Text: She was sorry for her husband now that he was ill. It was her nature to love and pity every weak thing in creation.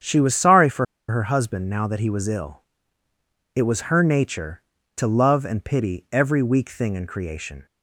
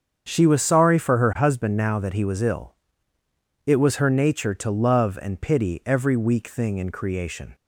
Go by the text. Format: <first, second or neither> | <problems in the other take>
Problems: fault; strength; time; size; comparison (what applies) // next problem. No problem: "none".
second | starts louder than the rest; strong; until 1.3 s; 8 dB; strong in the second // pauses between "for" and "her"; slight; at 0.8 s; 0.26 s long